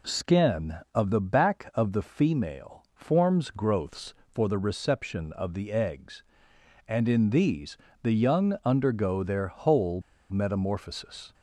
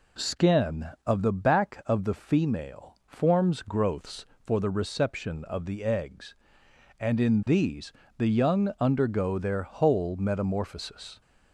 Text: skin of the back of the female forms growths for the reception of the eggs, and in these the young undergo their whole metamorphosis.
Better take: second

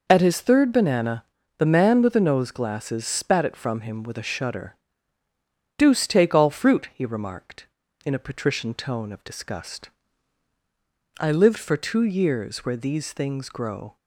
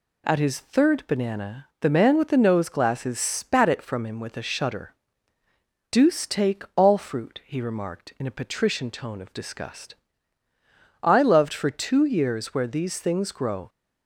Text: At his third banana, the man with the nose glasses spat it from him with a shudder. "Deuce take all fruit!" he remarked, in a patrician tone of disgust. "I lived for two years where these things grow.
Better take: first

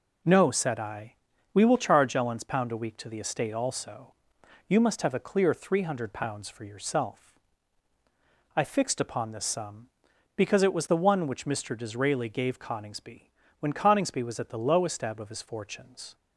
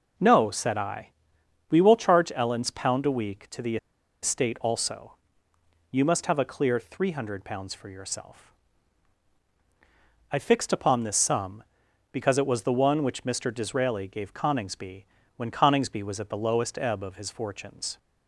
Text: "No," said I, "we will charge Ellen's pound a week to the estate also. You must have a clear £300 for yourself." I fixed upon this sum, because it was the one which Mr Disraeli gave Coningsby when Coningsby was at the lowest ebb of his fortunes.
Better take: first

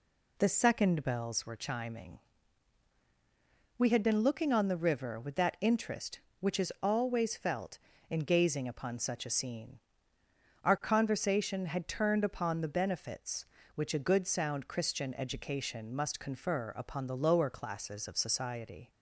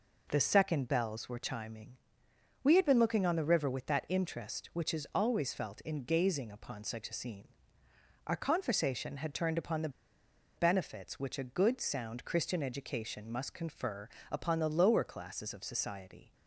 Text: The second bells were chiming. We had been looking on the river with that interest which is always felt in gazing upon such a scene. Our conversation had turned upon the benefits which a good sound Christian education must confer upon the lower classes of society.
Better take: first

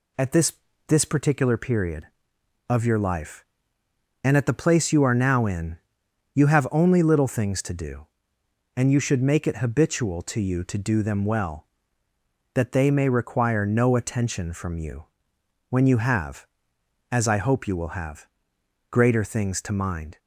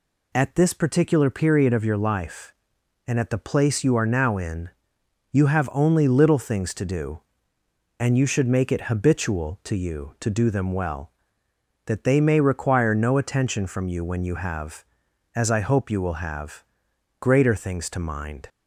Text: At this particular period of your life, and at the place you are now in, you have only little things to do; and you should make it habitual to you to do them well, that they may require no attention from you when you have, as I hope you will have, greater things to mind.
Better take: second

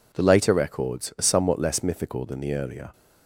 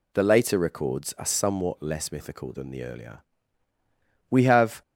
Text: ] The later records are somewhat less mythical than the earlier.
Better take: first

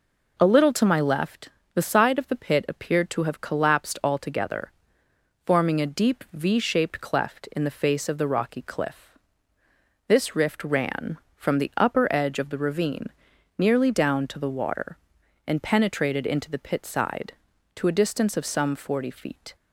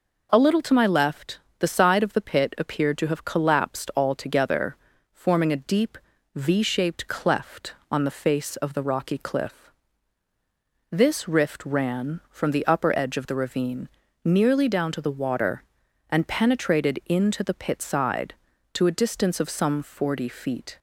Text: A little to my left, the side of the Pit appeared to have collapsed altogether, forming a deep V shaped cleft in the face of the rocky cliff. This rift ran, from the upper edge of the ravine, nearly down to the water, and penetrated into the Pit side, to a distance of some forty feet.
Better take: first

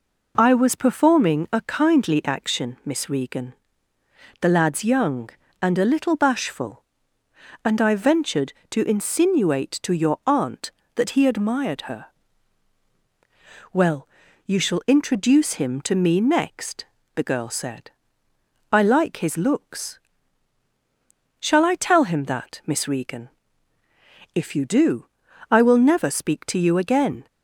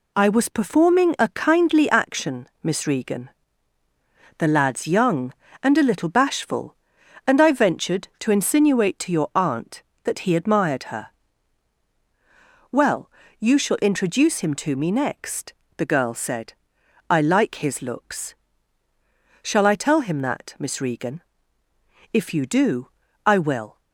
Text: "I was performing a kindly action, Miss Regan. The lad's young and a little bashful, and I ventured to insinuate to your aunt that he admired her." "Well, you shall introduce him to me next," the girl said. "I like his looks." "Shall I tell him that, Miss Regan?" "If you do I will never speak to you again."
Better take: first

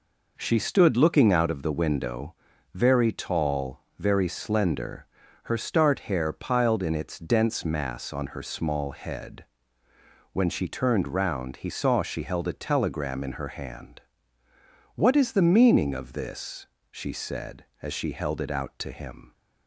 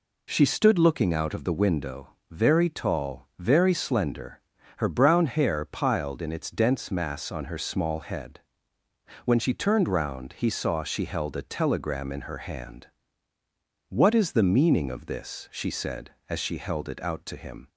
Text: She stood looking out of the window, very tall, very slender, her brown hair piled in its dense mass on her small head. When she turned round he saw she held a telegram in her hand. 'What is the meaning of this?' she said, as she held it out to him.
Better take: second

